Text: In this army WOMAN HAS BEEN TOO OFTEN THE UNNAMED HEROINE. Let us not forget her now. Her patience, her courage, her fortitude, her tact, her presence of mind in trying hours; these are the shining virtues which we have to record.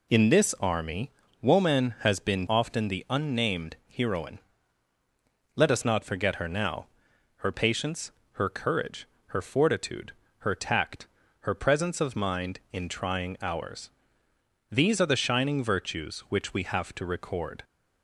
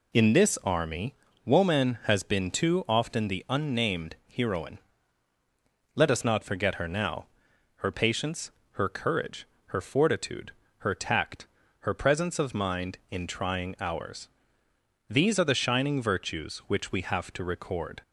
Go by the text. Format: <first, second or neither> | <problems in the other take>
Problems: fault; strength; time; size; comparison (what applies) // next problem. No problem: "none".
second | pauses between "army" and "WOMAN"; slight; at 1.1 s; 0.32 s long; slight in the second // skips "TOO"; at 2.4 s